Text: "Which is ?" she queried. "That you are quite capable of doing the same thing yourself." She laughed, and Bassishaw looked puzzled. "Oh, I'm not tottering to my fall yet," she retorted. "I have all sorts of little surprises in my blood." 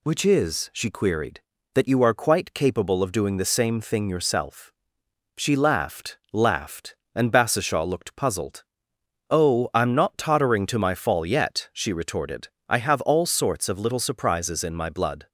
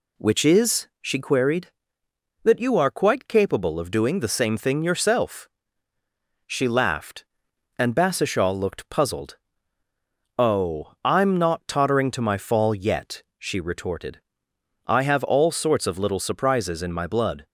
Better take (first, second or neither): second